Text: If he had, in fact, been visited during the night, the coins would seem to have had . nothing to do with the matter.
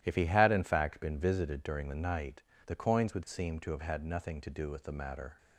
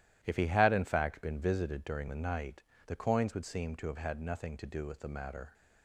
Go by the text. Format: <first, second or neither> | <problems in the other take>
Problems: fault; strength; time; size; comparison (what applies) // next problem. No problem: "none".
neither | starts louder than the rest; strong; the same in both